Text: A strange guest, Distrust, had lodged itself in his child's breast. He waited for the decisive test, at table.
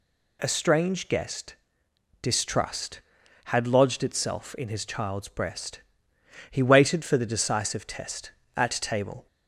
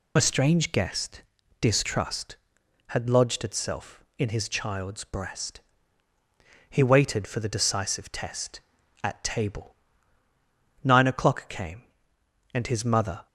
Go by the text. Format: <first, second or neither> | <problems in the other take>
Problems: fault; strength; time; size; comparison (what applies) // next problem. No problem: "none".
first | goes on to say "Nine o'clock came and his mother"; strong; from 10.8 s on; 2.4 s long